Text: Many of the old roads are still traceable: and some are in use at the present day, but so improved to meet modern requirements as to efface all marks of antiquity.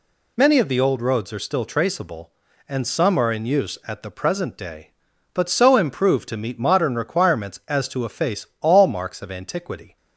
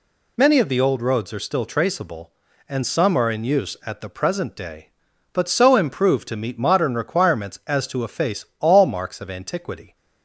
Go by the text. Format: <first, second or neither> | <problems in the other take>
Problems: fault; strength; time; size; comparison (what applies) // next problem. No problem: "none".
neither | none